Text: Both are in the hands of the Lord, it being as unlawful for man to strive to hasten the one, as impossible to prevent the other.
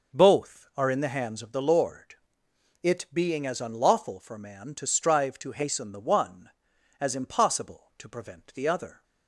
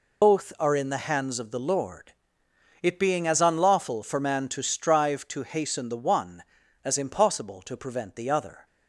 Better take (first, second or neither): first